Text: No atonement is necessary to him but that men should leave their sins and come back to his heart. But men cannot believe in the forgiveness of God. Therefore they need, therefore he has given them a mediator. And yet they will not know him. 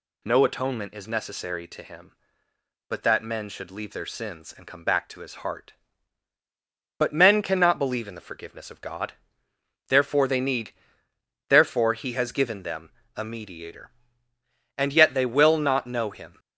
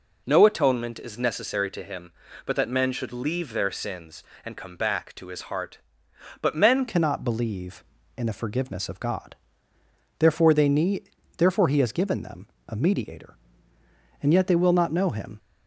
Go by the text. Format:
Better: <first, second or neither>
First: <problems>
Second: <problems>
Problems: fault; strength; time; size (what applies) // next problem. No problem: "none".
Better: first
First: pauses between "them" and "a"; slight; at 12.8 s; 0.26 s long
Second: changes voice at "cannot"; from 6.8 s on; 8.5 s long // pauses between "them" and "a"; slight; at 12.4 s; 0.20 s long